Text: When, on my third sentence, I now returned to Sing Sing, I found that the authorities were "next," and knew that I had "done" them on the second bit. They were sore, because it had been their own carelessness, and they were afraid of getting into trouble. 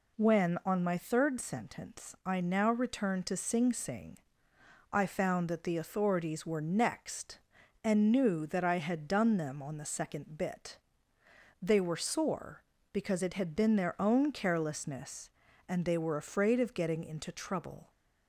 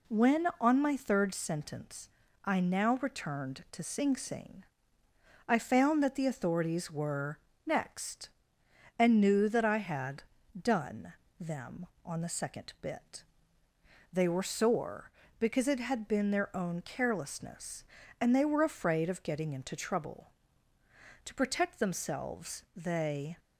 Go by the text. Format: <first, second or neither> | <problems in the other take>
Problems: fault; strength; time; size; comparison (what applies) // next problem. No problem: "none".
first | pauses between "were" and "next"; slight; at 7.3 s; 0.26 s long // pauses between "had" and "done"; at 10.2 s; 0.38 s long // pauses between "done" and "them"; slight; at 11.1 s; 0.26 s long // goes on to say "To protect themselves they"; strong; from 21.2 s on; 2.1 s long